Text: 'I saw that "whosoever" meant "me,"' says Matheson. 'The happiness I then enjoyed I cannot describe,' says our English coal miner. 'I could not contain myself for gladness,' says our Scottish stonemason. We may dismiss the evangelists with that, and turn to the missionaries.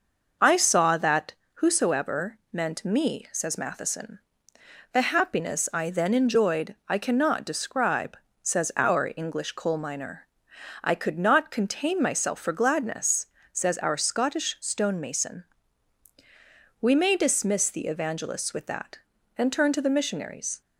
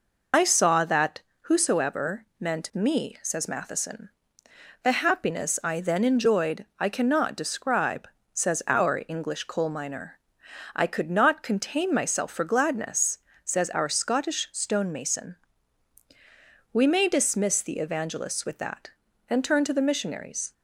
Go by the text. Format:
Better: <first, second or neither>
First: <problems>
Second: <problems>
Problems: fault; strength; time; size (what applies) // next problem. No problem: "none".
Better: first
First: pauses between "that" and "whosoever"; slight; at 1.3 s; 0.22 s long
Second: loses the start of "I"; at 0.3 s; 60 ms // pauses between "that" and "whosoever"; slight; at 1.1 s; 0.22 s long